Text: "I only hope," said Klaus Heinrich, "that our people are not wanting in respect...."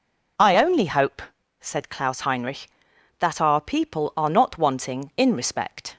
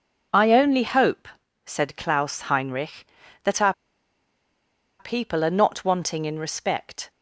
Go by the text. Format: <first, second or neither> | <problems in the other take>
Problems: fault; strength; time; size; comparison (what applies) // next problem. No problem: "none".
first | pauses between "our" and "people"; strong; at 3.7 s; 1.2 s long